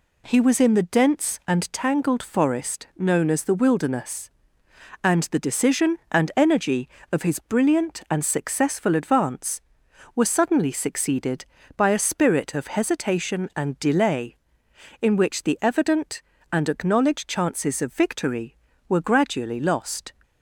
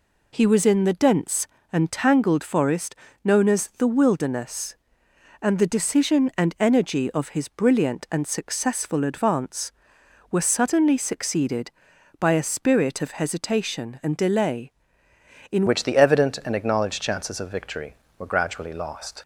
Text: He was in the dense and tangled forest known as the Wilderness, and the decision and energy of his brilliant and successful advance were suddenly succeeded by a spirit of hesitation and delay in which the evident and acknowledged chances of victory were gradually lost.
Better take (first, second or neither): first